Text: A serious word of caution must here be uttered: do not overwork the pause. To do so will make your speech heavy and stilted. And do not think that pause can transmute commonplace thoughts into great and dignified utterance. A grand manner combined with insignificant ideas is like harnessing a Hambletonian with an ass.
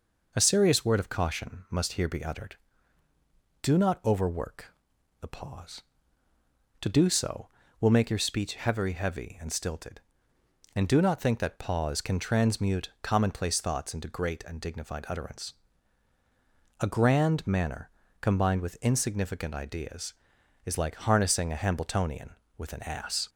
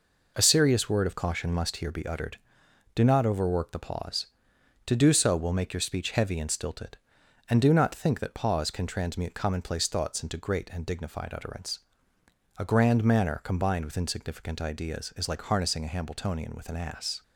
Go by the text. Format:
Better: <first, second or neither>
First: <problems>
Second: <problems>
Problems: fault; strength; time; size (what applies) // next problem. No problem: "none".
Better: second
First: pauses between "overwork" and "the"; noticeable; at 4.7 s; 0.48 s long // says "heavy" twice; at 8.9 s // pauses between "manner" and "combined"; slight; at 17.9 s; 0.32 s long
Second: none